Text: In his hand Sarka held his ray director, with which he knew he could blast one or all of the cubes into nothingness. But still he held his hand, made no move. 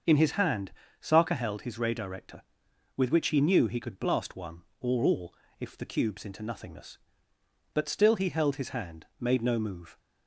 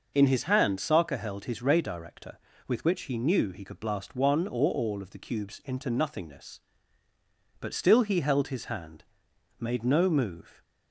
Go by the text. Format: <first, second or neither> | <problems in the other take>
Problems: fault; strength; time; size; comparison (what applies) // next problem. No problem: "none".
second | starts louder than the rest; until 1.3 s; 6.5 dB // pauses between "hand" and "Sarka"; slight; at 0.7 s; 0.28 s long // says "if" for "of"; at 5.5 s